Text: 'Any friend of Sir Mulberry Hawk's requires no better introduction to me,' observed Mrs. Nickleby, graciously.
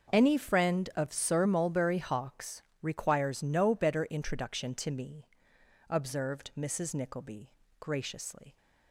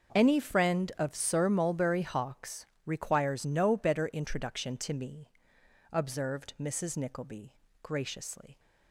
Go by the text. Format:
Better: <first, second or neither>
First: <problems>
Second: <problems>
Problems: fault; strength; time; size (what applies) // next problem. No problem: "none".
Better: neither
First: starts louder than the rest; until 1.1 s; 6.5 dB // pauses between "Hawk's" and "requires"; slight; at 2.6 s; 0.20 s long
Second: starts louder than the rest; until 1.1 s; 6.5 dB // pauses between "Hawk's" and "requires"; slight; at 2.6 s; 0.20 s long